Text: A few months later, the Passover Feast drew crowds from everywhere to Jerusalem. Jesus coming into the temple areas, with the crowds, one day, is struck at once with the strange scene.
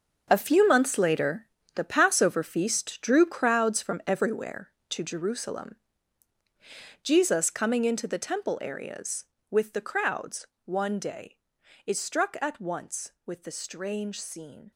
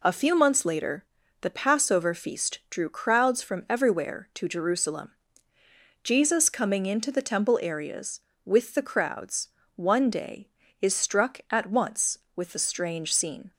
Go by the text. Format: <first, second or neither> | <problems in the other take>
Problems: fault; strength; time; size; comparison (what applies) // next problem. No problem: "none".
second | gets quieter; strong; throughout; 11.5 dB